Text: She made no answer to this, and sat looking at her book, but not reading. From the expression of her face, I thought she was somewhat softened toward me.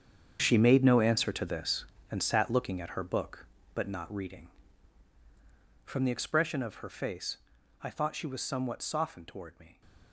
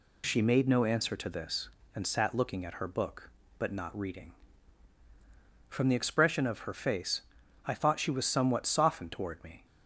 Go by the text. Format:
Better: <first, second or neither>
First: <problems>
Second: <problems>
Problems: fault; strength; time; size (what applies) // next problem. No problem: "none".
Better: second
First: gets quieter; strong; throughout; 13.5 dB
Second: none